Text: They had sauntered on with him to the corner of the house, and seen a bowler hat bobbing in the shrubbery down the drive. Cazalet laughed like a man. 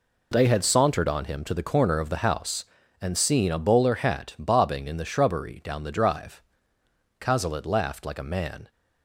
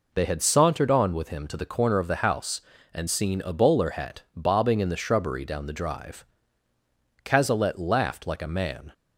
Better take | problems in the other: second | skips "with"; at 1.2 s

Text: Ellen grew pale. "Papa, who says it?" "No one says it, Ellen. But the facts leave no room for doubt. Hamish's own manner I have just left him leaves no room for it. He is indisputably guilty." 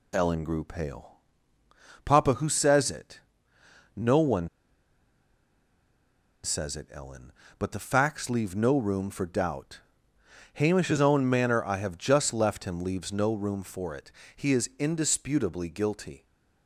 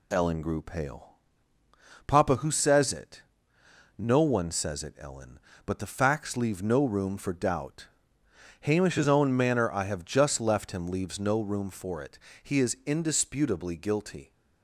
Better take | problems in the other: second | pauses between "one" and "says"; strong; at 4.4 s; 1.9 s long

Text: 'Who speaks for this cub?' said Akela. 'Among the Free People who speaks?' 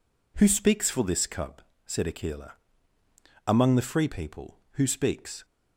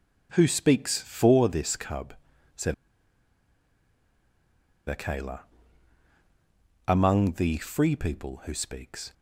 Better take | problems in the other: first | pauses between "said" and "Akela"; strong; at 2.7 s; 2.1 s long

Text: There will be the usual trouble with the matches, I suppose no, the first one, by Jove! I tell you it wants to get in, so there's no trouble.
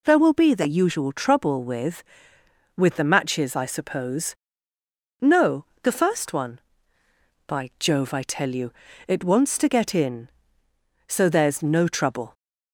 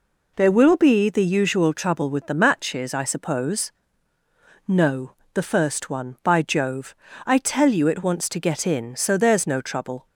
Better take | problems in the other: second | says "with" twice; at 2.7 s // pauses between "suppose" and "no"; noticeable; at 4.3 s; 0.90 s long; noticeable in the second // pauses between "you" and "it"; slight; at 8.7 s; 0.36 s long

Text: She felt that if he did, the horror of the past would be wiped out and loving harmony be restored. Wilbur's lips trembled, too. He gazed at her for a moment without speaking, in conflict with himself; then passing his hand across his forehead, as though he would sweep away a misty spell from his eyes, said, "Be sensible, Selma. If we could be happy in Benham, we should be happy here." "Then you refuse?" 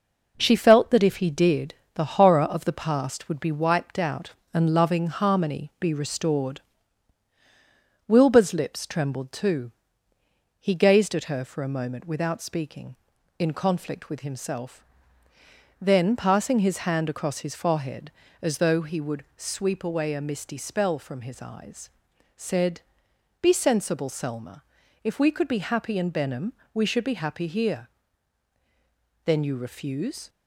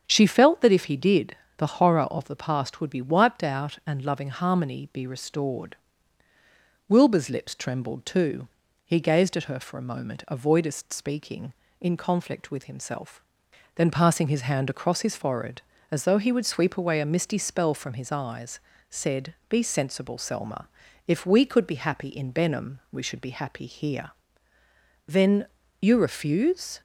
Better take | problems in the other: first | starts louder than the rest; strong; until 1.0 s; 8 dB // says "avoidest" for "without"; at 10.2 s // pauses between "Then" and "you"; slight; at 25.4 s; 0.34 s long

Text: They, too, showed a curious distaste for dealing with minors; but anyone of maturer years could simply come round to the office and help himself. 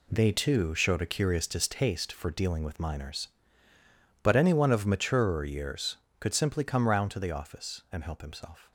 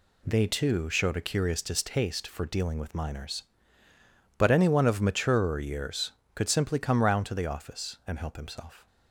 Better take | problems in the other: second | gets quieter; strong; throughout; 9 dB

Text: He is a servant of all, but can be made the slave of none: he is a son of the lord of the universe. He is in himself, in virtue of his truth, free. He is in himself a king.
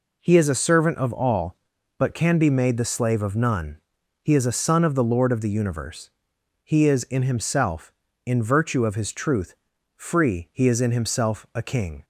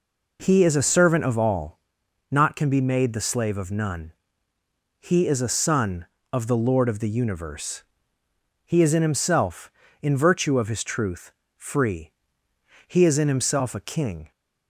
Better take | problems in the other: first | says "not" for "but"; at 2.3 s

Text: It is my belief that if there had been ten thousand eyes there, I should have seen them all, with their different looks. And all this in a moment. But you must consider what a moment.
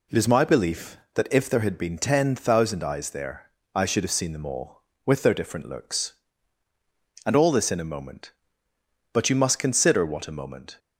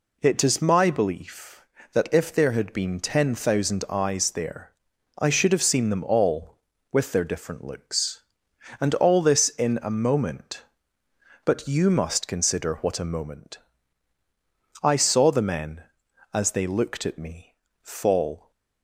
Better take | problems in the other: first | goes on to say "I saw the men as they looked at me fall"; strong; from 14.8 s on; 3.6 s long

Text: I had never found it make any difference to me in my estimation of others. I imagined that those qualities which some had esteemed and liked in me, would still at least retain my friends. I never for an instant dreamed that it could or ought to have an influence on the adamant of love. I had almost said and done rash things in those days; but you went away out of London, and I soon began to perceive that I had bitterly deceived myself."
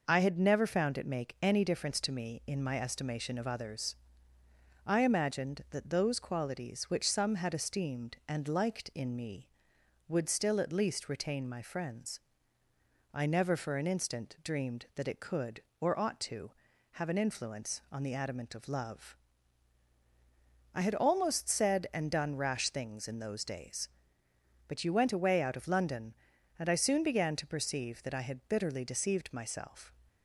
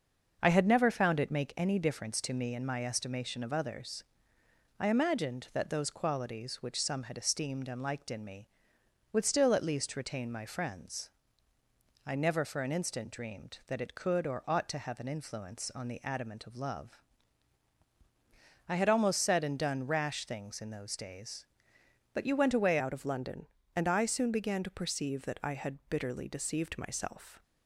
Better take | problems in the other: first | starts louder than the rest; until 1.4 s; 6 dB // changes voice at "out"; from 22.7 s on; 4.7 s long

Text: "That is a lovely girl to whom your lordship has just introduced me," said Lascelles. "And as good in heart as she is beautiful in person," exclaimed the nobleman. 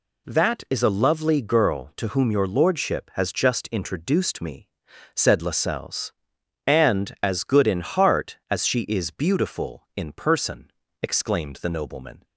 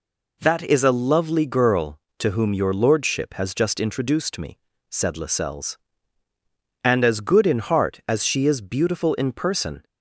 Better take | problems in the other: first | stops before "exclaimed the nobleman"; at 9.8 s

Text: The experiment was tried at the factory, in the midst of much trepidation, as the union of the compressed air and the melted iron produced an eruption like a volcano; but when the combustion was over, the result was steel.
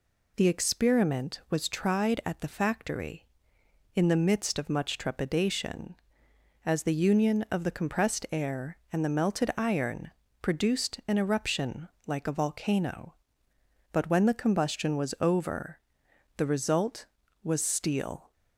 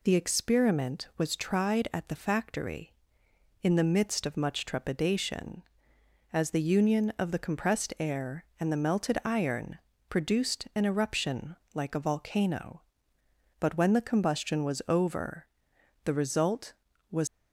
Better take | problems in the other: first | pauses between "iron" and "produced"; slight; at 9.7 s; 0.32 s long; slight in the first // pauses between "eruption" and "like"; slight; at 11.5 s; 0.20 s long; slight in the first // stops before "steel"; at 17.2 s

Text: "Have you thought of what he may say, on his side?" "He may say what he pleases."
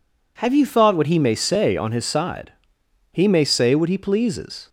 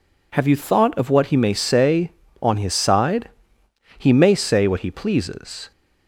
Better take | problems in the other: second | skips "of"; at 0.9 s

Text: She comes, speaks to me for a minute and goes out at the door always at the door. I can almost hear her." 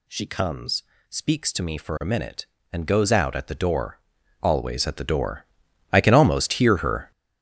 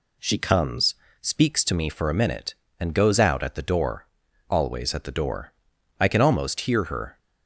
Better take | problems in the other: second | gets louder; strong; throughout; 10.5 dB // pauses between "door" and "always"; at 3.9 s; 0.44 s long; also in the second

